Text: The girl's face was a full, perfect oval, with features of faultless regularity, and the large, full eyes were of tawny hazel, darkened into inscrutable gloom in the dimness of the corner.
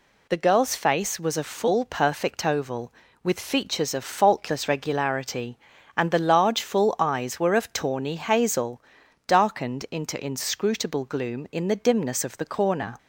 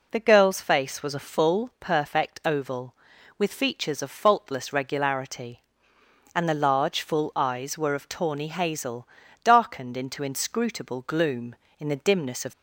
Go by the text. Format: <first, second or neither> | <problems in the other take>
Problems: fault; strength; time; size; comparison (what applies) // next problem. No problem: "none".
first | stops before "the corner"; at 12.5 s